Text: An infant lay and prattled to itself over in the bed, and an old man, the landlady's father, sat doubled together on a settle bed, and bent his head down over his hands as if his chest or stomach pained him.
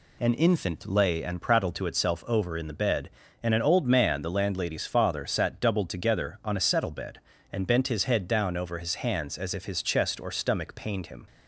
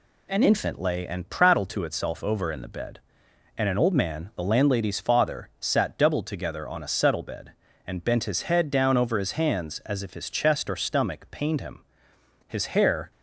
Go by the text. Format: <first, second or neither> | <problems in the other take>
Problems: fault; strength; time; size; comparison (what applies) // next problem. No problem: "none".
first | goes on to say "His hair"; noticeable; from 12.4 s on; 0.64 s long